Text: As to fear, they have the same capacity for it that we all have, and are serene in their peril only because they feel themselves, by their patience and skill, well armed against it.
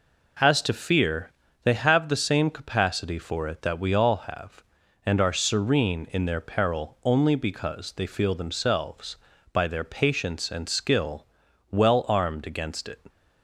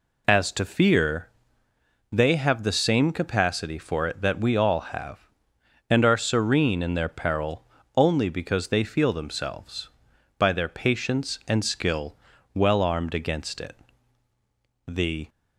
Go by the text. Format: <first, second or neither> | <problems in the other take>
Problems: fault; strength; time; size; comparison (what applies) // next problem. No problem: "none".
first | pauses between "peril" and "only"; slight; at 7.6 s; 0.32 s long // goes on to say "The"; slight; from 14.8 s on; 0.42 s long